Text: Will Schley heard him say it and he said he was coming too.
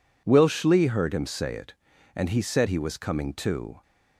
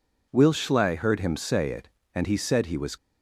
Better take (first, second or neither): first